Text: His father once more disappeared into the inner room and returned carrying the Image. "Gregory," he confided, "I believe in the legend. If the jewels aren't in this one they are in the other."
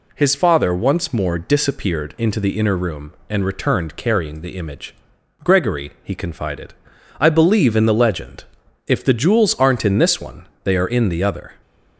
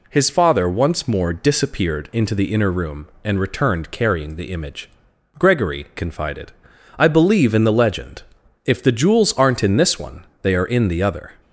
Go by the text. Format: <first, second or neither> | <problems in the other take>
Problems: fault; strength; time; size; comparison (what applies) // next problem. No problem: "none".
first | skips "he"; at 5.9 s // pauses between "one" and "they"; slight; at 10.2 s; 0.18 s long; slight in the first